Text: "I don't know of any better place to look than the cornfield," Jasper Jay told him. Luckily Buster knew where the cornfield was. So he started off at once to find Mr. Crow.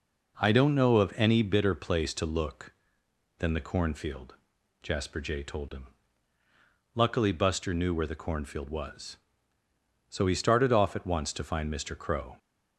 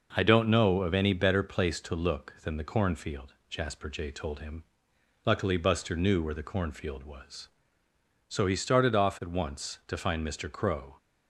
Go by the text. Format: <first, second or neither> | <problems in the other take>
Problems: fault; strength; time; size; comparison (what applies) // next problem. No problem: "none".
second | says "bitter" for "better"; at 1.4 s